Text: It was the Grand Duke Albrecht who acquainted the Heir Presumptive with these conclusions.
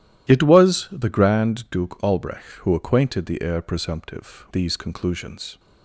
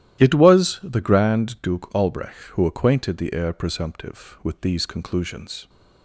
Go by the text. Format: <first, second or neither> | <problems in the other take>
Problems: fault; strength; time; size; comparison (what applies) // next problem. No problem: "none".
second | starts louder than the rest; strong; until 1.3 s; 13 dB; strong in the second // skips "with"; at 4.4 s